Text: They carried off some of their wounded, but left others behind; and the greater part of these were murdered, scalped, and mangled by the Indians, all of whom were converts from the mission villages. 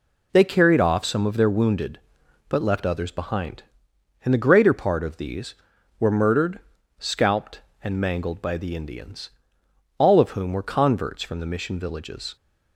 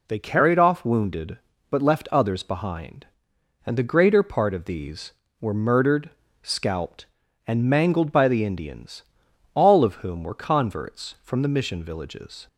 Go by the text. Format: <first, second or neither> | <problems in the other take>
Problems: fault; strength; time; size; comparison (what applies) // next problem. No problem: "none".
first | skips "some of their"; at 0.8 s